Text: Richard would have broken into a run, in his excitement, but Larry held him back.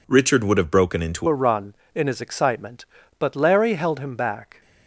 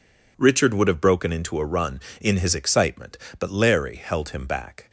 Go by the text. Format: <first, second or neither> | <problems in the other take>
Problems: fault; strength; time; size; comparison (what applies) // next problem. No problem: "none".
second | changes voice at "a"; from 1.2 s on; 3.4 s long